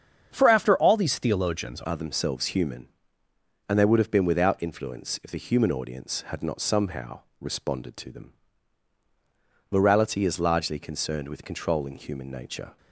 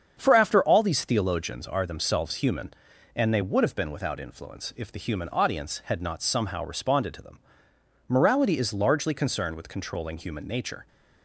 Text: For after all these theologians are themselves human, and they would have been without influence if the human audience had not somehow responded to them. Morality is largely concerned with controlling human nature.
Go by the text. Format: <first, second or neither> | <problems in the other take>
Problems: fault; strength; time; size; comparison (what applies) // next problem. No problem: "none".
second | starts louder than the rest; strong; until 1.3 s; 7.5 dB; strong in the second // changes voice at "are"; from 1.8 s on; 10.9 s long // pauses between "somehow" and "responded"; slight; at 7.2 s; 0.20 s long